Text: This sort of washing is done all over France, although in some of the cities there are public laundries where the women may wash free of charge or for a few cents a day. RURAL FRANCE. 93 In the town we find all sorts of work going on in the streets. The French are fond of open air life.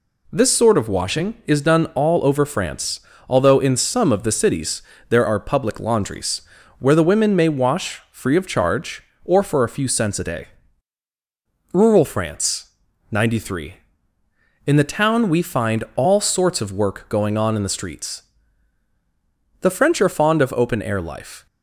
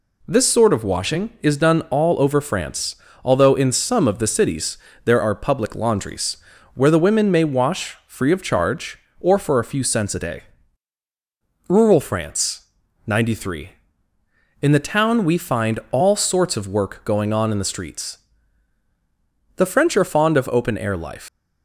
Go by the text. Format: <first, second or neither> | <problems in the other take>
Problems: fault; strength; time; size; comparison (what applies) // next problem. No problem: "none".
first | pauses between "cities" and "there"; slight; at 4.7 s; 0.26 s long; slight in the first // pauses between "laundries" and "where"; slight; at 6.3 s; 0.36 s long; slight in the first // leaves "life" unfinished; at 21.2 s; 130 ms